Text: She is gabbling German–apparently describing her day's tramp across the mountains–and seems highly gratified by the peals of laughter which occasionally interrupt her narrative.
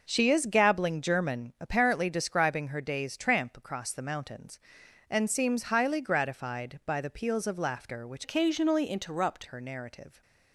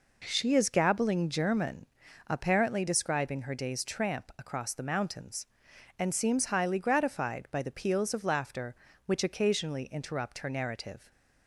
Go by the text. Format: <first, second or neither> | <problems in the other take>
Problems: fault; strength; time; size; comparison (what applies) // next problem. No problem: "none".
second | changes voice from "occasionally" to "interrupt"; from 8.2 to 9.4 s; 1.2 s long